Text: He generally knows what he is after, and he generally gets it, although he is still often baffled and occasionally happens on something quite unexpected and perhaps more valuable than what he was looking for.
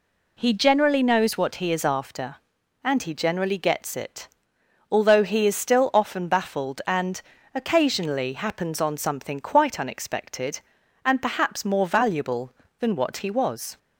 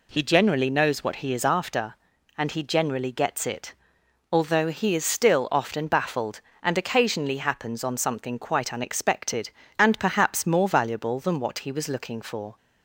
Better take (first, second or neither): second